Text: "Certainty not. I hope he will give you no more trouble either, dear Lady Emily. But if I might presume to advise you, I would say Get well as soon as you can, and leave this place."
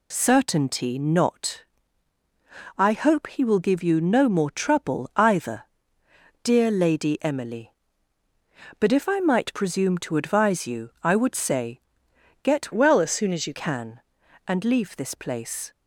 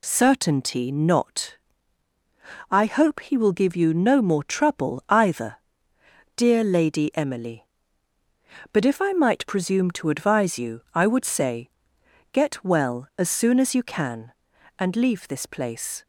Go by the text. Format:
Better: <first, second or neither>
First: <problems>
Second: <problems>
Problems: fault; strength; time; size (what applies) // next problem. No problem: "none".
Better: second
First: pauses between "say" and "Get"; noticeable; at 11.7 s; 0.64 s long // changes voice from "well" to "you"; from 12.7 to 13.5 s; 0.8 s long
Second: pauses between "say" and "Get"; noticeable; at 11.6 s; 0.64 s long